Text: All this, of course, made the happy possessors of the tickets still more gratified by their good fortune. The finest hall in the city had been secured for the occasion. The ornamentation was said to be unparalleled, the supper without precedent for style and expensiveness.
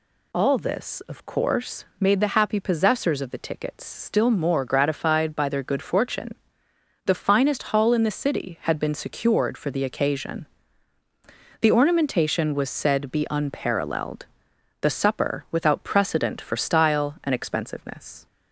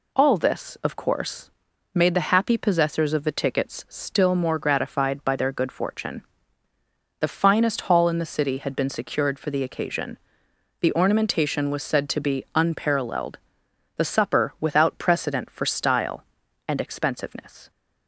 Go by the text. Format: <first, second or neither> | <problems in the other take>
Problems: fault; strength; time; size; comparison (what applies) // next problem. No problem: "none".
second | skips "to"; at 13.1 s